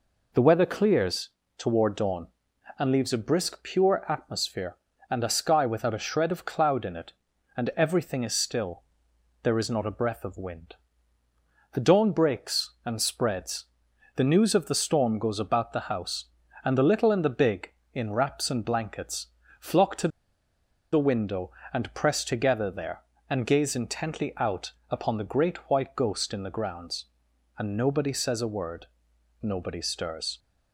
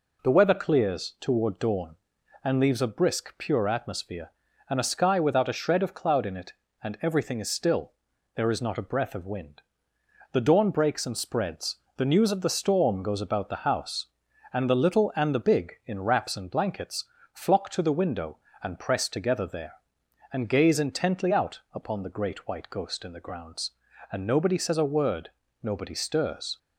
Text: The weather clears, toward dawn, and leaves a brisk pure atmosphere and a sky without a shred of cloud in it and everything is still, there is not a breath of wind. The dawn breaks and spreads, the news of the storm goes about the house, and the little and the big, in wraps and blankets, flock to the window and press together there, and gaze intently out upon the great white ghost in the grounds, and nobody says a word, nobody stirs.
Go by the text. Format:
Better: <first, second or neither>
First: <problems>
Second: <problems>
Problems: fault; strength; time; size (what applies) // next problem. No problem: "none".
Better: second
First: pauses between "to" and "the"; noticeable; at 20.0 s; 0.84 s long // pauses between "out" and "upon"; slight; at 24.7 s; 0.16 s long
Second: none